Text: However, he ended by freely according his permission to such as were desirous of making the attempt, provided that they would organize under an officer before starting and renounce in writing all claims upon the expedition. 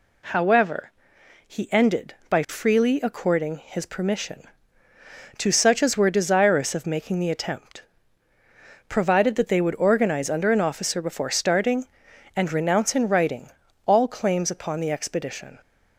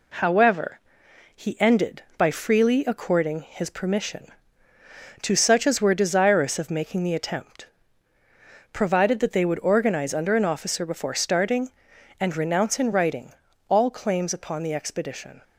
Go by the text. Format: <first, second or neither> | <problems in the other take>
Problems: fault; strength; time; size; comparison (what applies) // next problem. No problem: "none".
first | gets quieter; slight; throughout; 2 dB // pauses between "writing" and "all"; slight; at 13.3 s; 0.36 s long; slight in the first